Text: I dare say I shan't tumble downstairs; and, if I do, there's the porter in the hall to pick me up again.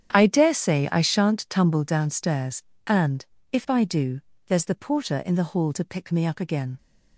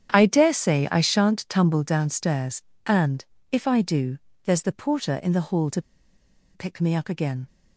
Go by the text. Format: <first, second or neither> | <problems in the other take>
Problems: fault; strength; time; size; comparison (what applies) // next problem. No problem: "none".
first | starts louder than the rest; strong; until 1.1 s; 9 dB; strong in the first // pauses between "to" and "pick"; noticeable; at 5.8 s; 0.73 s long